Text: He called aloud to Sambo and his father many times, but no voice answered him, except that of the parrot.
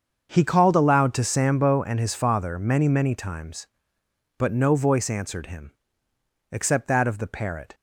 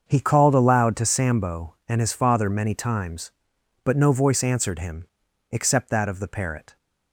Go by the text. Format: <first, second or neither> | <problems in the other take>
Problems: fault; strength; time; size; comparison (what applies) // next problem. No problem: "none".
second | starts louder than the rest; until 1.3 s; 7 dB; also in the second // says "many" twice; at 2.8 s